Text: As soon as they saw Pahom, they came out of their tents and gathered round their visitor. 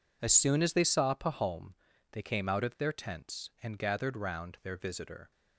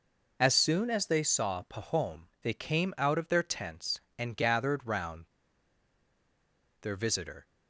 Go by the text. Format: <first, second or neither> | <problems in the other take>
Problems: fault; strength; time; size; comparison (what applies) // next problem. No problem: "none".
first | pauses between "round" and "their"; strong; at 5.2 s; 1.5 s long